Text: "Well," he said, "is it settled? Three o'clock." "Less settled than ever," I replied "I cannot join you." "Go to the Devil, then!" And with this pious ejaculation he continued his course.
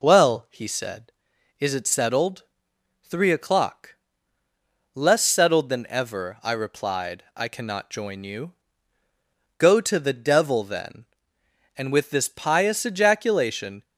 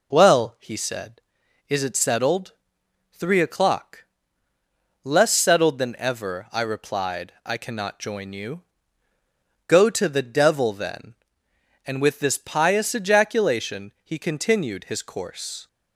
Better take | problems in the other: second | stops before "he continued his course"; at 13.8 s

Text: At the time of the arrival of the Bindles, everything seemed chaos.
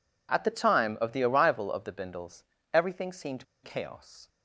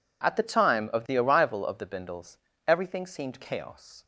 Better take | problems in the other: second | pauses between "seemed" and "chaos"; slight; at 3.4 s; 0.21 s long

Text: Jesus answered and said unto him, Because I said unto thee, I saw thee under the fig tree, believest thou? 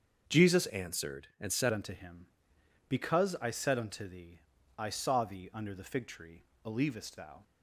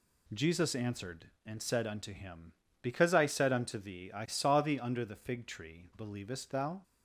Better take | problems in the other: second | starts louder than the rest; until 1.4 s; 7 dB // changes voice from "answered" to "said"; from 0.6 to 1.7 s; 1.1 s long

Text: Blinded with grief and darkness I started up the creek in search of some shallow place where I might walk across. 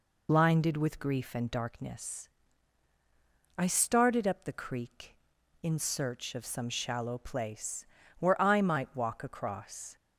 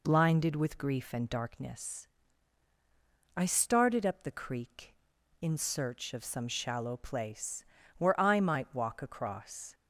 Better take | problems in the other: second | loses the start of "Blinded"; at 0.2 s; 30 ms // pauses between "darkness" and "I"; strong; at 2.2 s; 1.3 s long; strong in the second // pauses between "place" and "where"; slight; at 7.8 s; 0.34 s long; slight in the second

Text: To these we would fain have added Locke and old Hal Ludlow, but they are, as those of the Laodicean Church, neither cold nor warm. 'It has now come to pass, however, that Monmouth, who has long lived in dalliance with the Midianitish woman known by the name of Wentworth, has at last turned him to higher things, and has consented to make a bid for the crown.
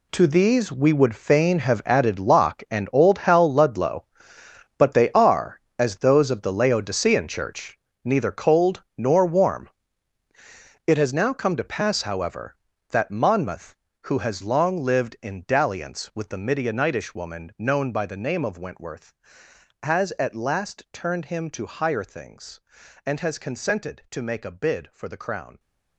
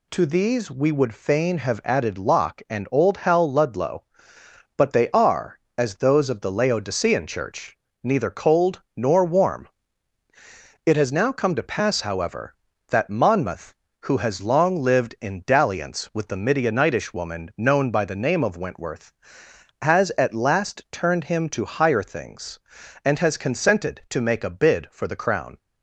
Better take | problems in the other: second | gets quieter; strong; throughout; 13 dB

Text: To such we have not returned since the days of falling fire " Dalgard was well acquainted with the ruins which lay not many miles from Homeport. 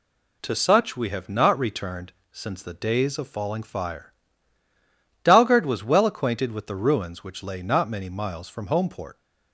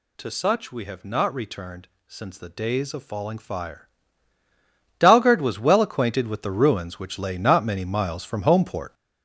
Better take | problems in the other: first | gets louder; throughout; 6.5 dB // pauses between "returned" and "since"; slight; at 1.8 s; 0.20 s long; slight in the first

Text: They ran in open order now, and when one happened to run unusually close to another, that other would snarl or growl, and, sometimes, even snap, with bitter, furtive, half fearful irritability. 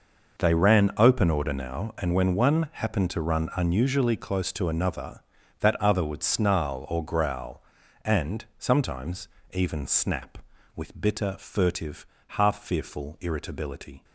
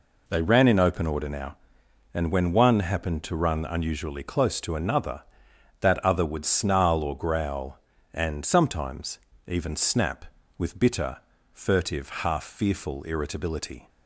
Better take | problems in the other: second | skips "in"; at 0.9 s

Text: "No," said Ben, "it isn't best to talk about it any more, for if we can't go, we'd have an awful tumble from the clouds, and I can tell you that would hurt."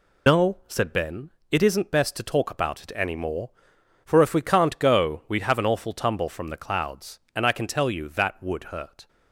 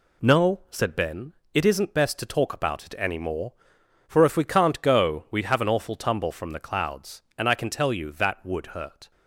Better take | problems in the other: second | loses the start of "No"; at 0.2 s; 75 ms

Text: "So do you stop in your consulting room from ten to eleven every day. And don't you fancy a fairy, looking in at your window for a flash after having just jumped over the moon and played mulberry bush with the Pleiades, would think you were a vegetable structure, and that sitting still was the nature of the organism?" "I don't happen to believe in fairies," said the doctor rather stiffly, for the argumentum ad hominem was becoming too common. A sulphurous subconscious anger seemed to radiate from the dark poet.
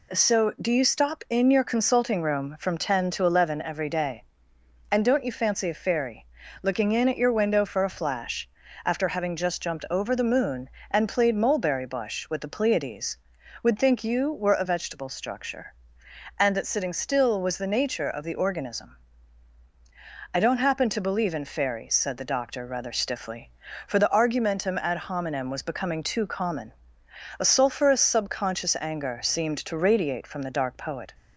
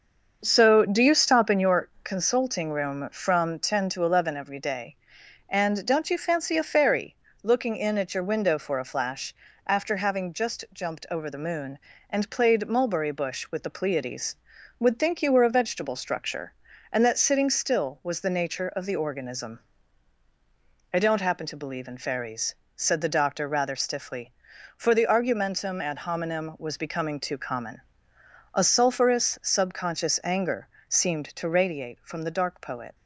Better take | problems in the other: first | starts louder than the rest; until 1.9 s; 6.5 dB // pauses between "your" and "consulting"; slight; at 1.8 s; 0.16 s long // pauses between "flash" and "after"; slight; at 9.3 s; 0.32 s long; also in the first // pauses between "anger" and "seemed"; slight; at 30.6 s; 0.22 s long

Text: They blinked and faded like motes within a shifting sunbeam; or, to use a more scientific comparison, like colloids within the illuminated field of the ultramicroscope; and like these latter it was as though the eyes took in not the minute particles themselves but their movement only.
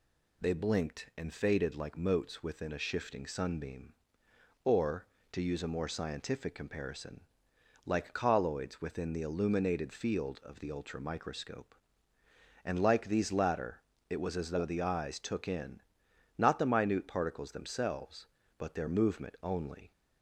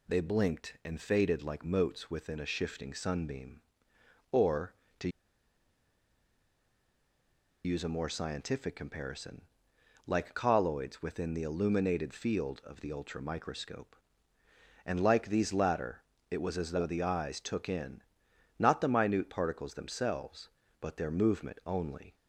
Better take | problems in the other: first | pauses between "to" and "use"; strong; at 5.0 s; 2.5 s long // pauses between "latter" and "it"; slight; at 16.0 s; 0.26 s long; slight in the first // pauses between "in" and "not"; noticeable; at 18.0 s; 0.56 s long; noticeable in the first

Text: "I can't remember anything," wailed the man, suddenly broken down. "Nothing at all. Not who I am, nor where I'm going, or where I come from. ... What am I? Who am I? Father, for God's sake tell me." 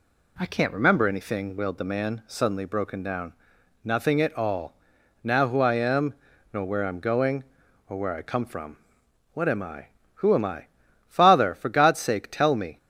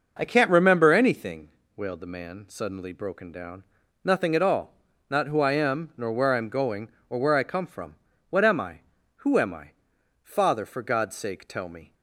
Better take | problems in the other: second | says "Now" for "Not"; at 5.2 s

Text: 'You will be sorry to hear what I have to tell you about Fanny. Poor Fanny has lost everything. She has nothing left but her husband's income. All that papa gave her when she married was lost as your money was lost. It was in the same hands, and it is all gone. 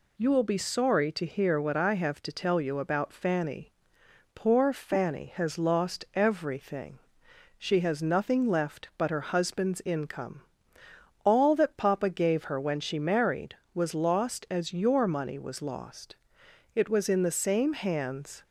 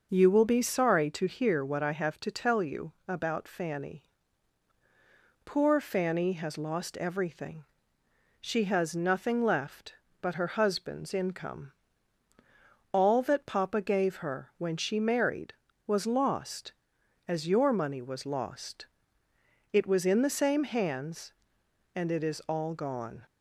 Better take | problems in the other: second | stops before "and it is all gone"; at 18.4 s

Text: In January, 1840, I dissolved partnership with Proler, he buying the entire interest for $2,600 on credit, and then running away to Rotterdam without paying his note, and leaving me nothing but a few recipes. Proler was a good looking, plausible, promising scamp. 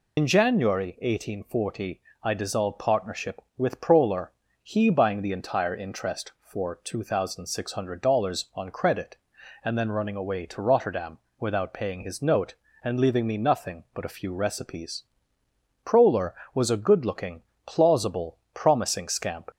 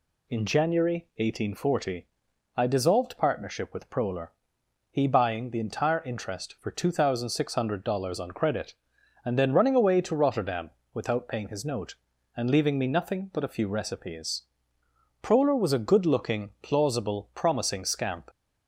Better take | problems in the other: second | loses the start of "In"; at 0.1 s; 90 ms // pauses between "Rotterdam" and "without"; slight; at 11.1 s; 0.22 s long; slight in the second

